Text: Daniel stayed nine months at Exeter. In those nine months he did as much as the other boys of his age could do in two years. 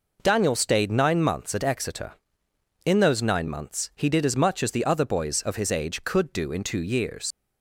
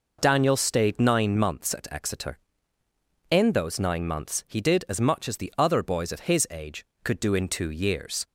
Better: second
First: leaves "years" unfinished; at 7.3 s; 70 ms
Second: none

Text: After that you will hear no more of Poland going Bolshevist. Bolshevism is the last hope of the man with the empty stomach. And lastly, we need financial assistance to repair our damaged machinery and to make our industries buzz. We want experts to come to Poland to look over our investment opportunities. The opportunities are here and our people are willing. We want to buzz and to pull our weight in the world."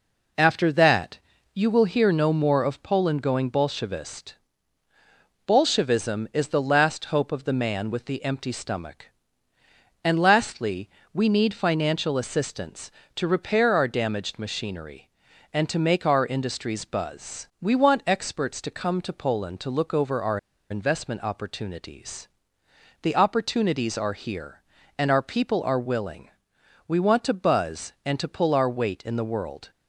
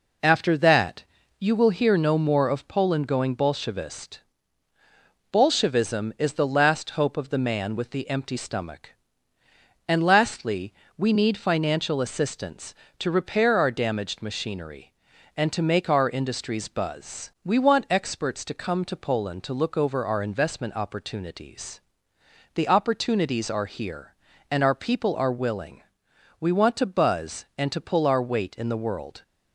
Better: second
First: pauses between "that" and "you"; slight; at 1.1 s; 0.34 s long // pauses between "our" and "investment"; slight; at 20.3 s; 0.33 s long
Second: pauses between "that" and "you"; slight; at 1.0 s; 0.34 s long

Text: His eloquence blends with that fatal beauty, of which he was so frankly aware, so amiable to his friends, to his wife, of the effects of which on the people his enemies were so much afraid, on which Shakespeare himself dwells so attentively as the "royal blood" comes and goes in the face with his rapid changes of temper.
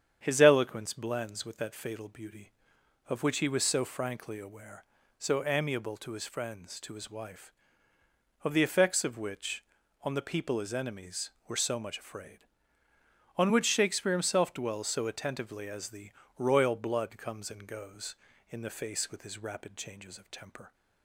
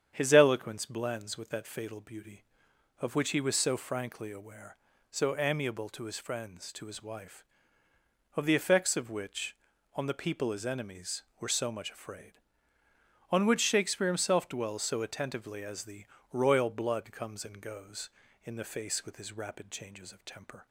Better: neither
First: starts louder than the rest; strong; until 1.2 s; 8.5 dB // pauses between "the" and "royal"; slight; at 16.1 s; 0.26 s long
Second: starts louder than the rest; strong; until 1.1 s; 8.5 dB // pauses between "the" and "royal"; slight; at 16.0 s; 0.26 s long

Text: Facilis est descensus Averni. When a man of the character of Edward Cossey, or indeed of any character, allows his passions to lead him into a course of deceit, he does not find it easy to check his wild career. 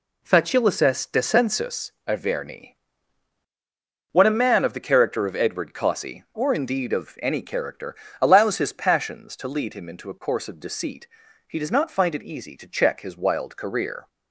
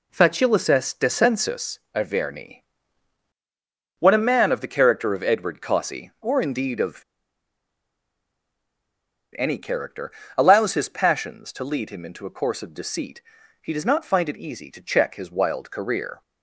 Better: first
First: pauses between "descensus" and "Averni"; slight; at 1.9 s; 0.16 s long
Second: pauses between "descensus" and "Averni"; slight; at 1.7 s; 0.16 s long // pauses between "of" and "any"; strong; at 7.0 s; 2.3 s long

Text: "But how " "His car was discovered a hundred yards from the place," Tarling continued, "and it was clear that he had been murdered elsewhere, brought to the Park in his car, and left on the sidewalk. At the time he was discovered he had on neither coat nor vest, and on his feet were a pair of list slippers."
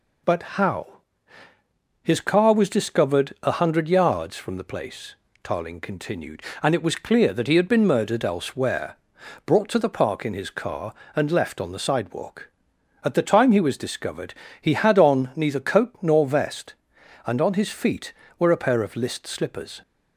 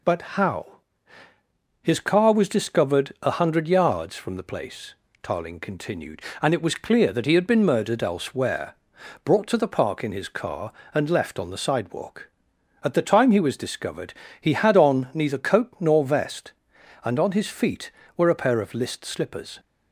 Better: neither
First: pauses between "discovered" and "he"; slight; at 14.3 s; 0.28 s long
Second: pauses between "discovered" and "he"; slight; at 14.1 s; 0.28 s long

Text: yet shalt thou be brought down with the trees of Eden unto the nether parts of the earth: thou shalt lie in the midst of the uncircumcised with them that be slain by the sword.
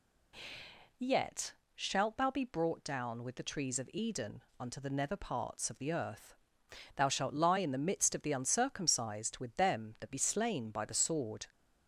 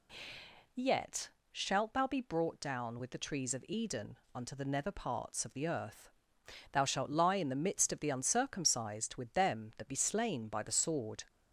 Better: neither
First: pauses between "yet" and "shalt"; slight; at 1.5 s; 0.22 s long // pauses between "Eden" and "unto"; slight; at 4.4 s; 0.18 s long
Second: pauses between "yet" and "shalt"; slight; at 1.2 s; 0.22 s long // pauses between "Eden" and "unto"; slight; at 4.1 s; 0.18 s long

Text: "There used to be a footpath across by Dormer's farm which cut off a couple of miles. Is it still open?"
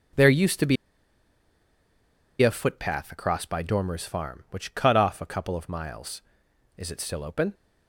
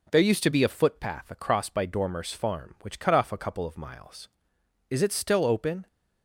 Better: second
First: pauses between "be" and "a"; strong; at 0.7 s; 1.6 s long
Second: none

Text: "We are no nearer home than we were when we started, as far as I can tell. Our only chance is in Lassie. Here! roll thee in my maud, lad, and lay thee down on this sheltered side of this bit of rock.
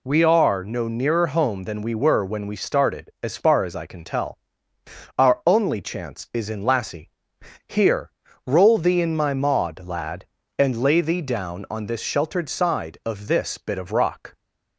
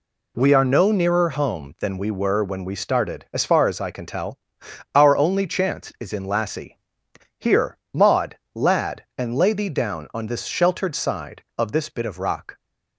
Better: first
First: none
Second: skips "roll thee in my"; at 7.8 s

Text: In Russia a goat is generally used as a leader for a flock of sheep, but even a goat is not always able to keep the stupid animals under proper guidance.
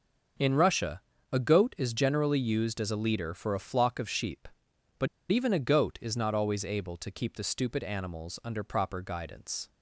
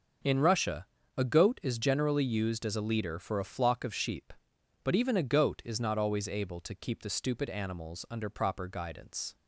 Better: second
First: starts louder than the rest; noticeable; until 1.7 s; 6 dB // pauses between "Russia" and "a"; slight; at 1.0 s; 0.32 s long // pauses between "but" and "even"; slight; at 5.0 s; 0.24 s long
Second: starts louder than the rest; noticeable; until 1.5 s; 6 dB // pauses between "Russia" and "a"; slight; at 0.8 s; 0.32 s long

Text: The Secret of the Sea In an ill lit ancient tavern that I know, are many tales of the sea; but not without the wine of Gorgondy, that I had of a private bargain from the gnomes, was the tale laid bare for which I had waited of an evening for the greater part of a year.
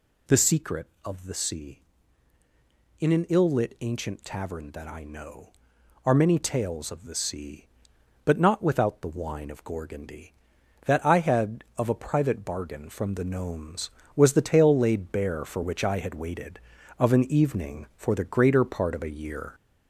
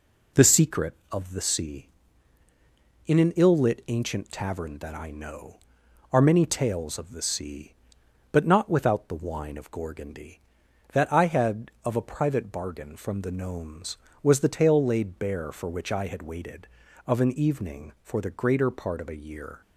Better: second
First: gets louder; noticeable; throughout; 4 dB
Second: none

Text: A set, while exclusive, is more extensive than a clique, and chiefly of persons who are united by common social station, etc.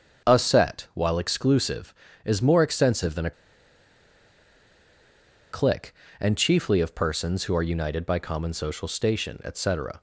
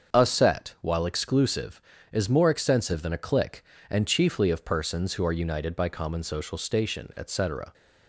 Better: second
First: starts louder than the rest; until 1.3 s; 7 dB // pauses between "a" and "clique"; strong; at 3.3 s; 2.2 s long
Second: starts louder than the rest; until 1.1 s; 7 dB

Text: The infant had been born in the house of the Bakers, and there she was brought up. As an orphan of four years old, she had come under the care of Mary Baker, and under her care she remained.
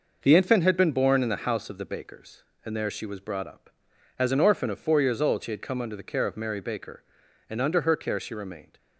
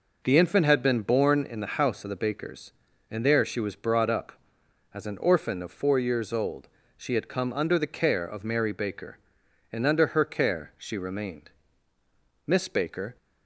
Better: first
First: none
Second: goes on to say "Miss Baker"; noticeable; from 12.4 s on; 0.70 s long

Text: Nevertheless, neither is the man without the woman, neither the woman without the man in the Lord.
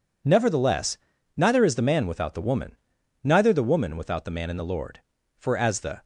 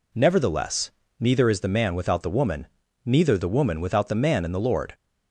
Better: second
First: goes on to say "For as the"; noticeable; from 5.3 s on; 0.66 s long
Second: none

